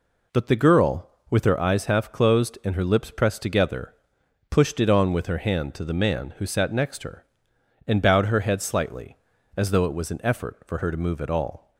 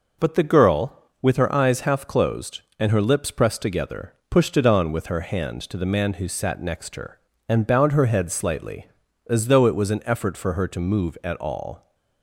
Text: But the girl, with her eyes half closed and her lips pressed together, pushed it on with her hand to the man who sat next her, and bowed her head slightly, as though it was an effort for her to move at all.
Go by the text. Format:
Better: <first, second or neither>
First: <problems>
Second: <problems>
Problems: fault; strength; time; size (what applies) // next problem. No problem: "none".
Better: neither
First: none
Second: none